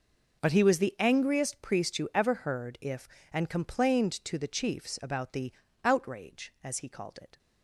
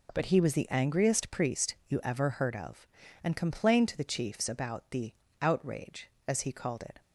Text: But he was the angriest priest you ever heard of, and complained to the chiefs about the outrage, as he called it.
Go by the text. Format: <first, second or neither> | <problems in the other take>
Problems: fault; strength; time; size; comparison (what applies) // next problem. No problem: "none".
second | says "if" for "of"; at 2.8 s // pauses between "the" and "outrage"; slight; at 5.5 s; 0.32 s long; slight in the second